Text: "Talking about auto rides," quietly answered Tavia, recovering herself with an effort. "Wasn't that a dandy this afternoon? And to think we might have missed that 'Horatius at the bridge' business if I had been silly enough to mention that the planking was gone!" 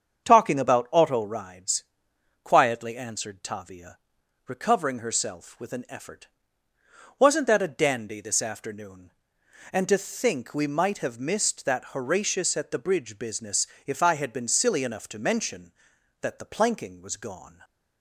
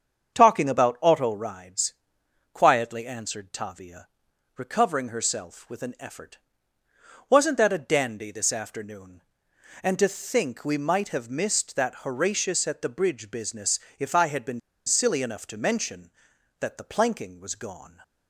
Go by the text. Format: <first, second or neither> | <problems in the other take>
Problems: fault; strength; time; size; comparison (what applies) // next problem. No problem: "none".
first | starts louder than the rest; strong; until 1.3 s; 7.5 dB; strong in the first // pauses between "business" and "if"; slight; at 13.8 s; 0.18 s long; slight in the first // pauses between "been" and "silly"; slight; at 14.6 s; 0.26 s long